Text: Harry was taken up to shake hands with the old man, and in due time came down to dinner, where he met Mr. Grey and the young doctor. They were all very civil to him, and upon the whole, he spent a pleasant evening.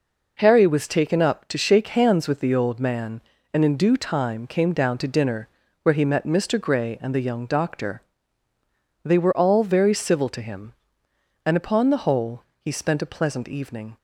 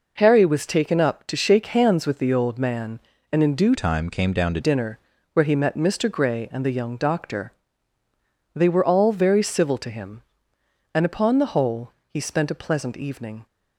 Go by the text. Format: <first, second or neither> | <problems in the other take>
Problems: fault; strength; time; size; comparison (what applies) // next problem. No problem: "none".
first | changes voice from "time" to "to"; from 3.7 to 4.5 s; 0.8 s long